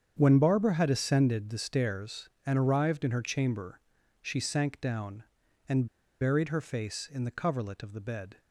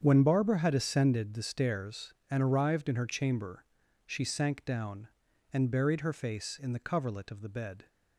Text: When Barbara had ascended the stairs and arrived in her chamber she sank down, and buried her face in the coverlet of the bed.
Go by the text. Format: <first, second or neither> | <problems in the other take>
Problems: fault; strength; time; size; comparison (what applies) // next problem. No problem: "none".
second | starts louder than the rest; strong; until 1.1 s; 7.5 dB; strong in the second // pauses between "chamber" and "she"; at 3.7 s; 0.40 s long; also in the second // pauses between "and" and "buried"; slight; at 5.8 s; 0.35 s long